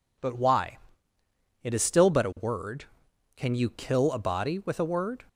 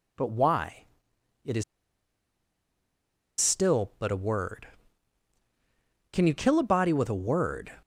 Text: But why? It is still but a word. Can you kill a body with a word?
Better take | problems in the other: first | pauses between "is" and "still"; strong; at 1.6 s; 1.7 s long

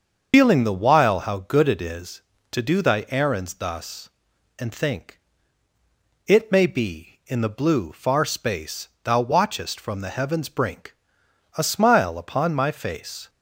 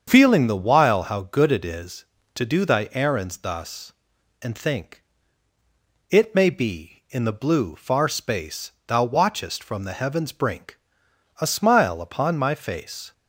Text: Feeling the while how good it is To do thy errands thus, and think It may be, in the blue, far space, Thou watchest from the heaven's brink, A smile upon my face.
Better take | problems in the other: second | loses the start of "Feeling"; at 0.3 s; 95 ms // starts louder than the rest; until 1.3 s; 6.5 dB; strong in the second // pauses between "think" and "It"; at 5.1 s; 1.0 s long; also in the second

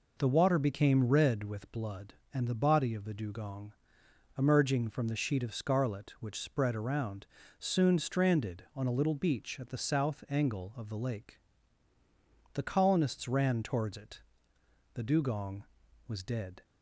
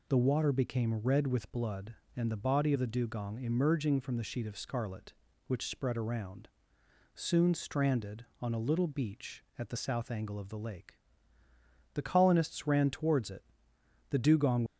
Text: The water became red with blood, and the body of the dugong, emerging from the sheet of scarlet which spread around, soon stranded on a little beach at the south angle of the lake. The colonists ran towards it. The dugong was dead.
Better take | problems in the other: first | stops before "was dead"; at 14.6 s

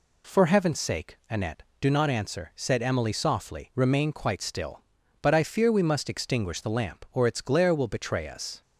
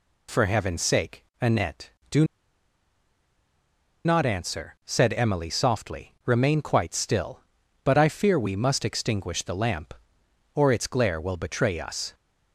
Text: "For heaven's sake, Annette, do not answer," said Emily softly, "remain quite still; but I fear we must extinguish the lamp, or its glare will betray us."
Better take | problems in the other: first | pauses between "do" and "not"; strong; at 2.2 s; 1.8 s long

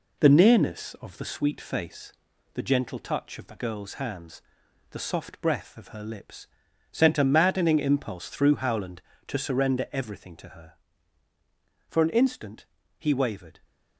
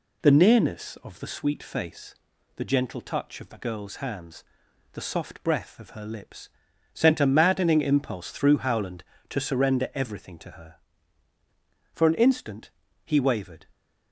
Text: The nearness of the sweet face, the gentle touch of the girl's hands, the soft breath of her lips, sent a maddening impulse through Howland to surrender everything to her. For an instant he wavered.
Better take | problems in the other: second | gets quieter; slight; throughout; 3 dB // pauses between "instant" and "he"; slight; at 12.6 s; 0.32 s long; slight in the second

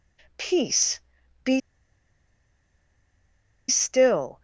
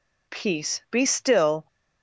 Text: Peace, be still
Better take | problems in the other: second | pauses between "be" and "still"; strong; at 1.6 s; 2.0 s long

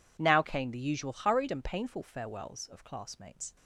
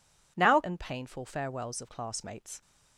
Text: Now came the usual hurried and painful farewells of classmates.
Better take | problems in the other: first | skips "came the usual hurried"; at 0.6 s

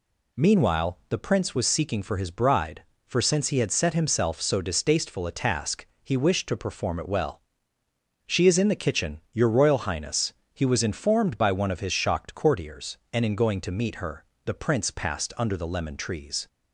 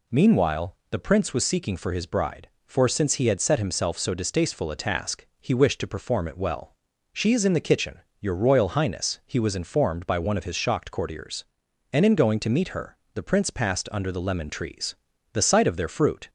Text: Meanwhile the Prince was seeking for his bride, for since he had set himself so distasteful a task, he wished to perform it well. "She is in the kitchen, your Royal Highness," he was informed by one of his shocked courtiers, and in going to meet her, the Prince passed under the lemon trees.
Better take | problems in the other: first | pauses between "Meanwhile" and "the"; slight; at 0.7 s; 0.16 s long // goes on to say "The sight of their fruit"; noticeable; from 15.3 s on; 0.96 s long

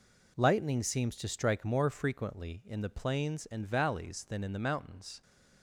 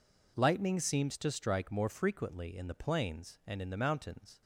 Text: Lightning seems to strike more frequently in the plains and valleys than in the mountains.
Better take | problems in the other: first | skips "valleys than"; at 3.6 s

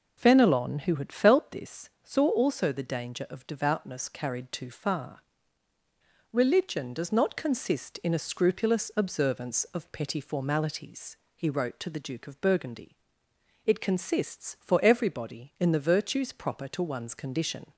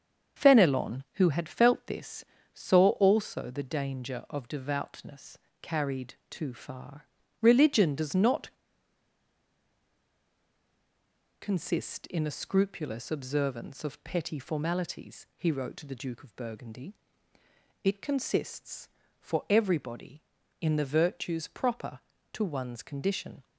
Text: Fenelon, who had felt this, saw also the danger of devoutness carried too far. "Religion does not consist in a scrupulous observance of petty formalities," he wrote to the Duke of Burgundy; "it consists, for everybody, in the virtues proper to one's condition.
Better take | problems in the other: first | starts louder than the rest; strong; until 1.4 s; 7 dB // pauses between "devoutness" and "carried"; slight; at 5.3 s; 0.22 s long // pauses between "carried" and "too"; slight; at 6.1 s; 0.16 s long // pauses between "not" and "consist"; strong; at 8.5 s; 2.8 s long

